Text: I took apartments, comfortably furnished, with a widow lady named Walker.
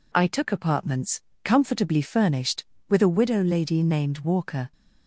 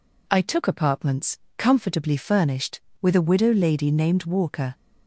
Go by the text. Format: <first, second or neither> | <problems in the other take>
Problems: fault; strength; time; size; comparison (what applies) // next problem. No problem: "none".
neither | none